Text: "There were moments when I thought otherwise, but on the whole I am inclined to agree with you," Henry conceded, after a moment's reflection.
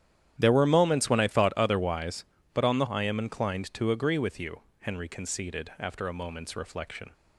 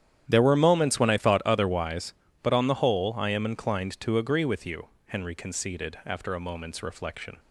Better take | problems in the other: second | starts louder than the rest; strong; until 1.3 s; 10.5 dB; strong in the second // skips "whole"; at 2.8 s

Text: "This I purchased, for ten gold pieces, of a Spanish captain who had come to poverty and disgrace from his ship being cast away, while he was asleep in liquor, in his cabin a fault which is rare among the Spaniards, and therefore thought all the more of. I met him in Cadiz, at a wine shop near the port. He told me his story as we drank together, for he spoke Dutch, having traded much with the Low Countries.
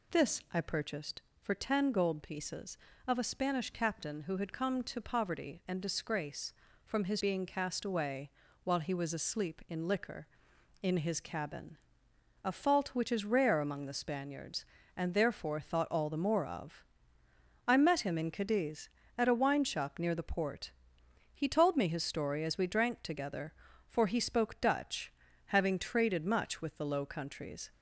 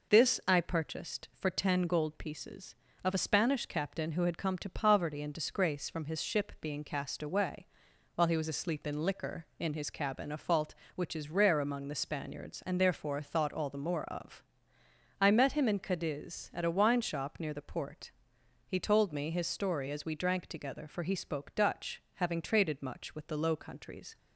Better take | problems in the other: second | skips "ship"; at 7.2 s // pauses between "cabin" and "a"; noticeable; at 11.7 s; 0.66 s long

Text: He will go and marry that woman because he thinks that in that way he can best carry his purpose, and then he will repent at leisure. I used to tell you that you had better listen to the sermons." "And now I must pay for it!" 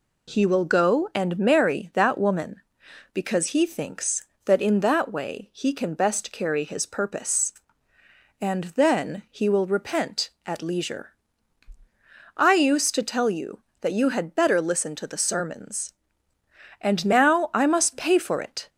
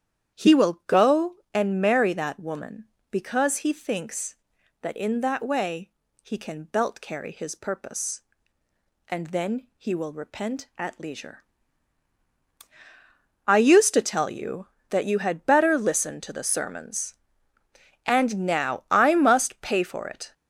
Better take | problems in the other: first | starts louder than the rest; strong; until 1.5 s; 9.5 dB // pauses between "way" and "he"; slight; at 5.9 s; 0.32 s long // says "belt" for "best"; at 6.6 s

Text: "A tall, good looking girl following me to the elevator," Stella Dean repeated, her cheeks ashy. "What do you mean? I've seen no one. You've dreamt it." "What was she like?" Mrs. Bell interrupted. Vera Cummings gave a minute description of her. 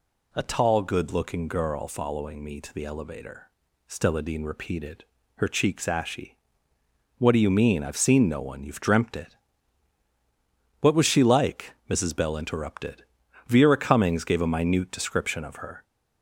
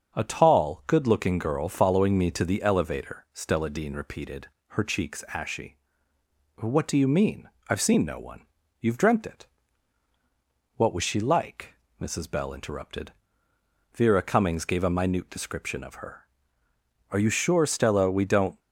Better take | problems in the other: first | starts louder than the rest; until 1.1 s; 7 dB // goes on to say "Are you sure Stella we don't"; from 17.1 s on; 1.4 s long

